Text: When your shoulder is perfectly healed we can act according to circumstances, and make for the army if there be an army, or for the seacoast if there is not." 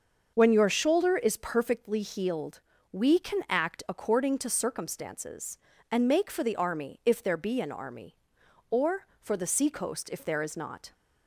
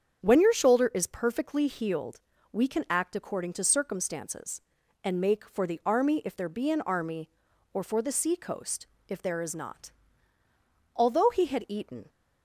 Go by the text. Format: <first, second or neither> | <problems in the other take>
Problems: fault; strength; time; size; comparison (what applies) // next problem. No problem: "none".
first | starts louder than the rest; strong; until 1.2 s; 7.5 dB; also in the first // pauses between "healed" and "we"; slight; at 2.1 s; 0.32 s long; slight in the first // pauses between "seacoast" and "if"; slight; at 8.8 s; 0.22 s long // goes on to say "Although he had eaten"; noticeable; from 10.9 s on; 1.1 s long